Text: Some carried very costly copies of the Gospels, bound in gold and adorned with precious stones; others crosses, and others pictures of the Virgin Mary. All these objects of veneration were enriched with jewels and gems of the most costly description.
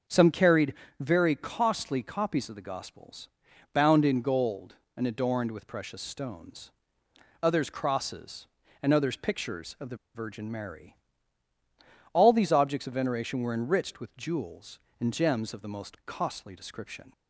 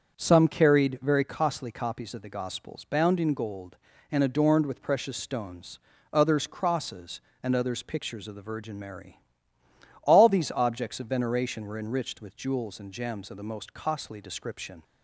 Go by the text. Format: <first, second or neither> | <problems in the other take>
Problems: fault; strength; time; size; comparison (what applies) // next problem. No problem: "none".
second | starts louder than the rest; noticeable; until 1.3 s; 6 dB; also in the second // pauses between "carried" and "very"; slight; at 0.7 s; 0.26 s long // pauses between "the" and "Virgin"; slight; at 9.9 s; 0.17 s long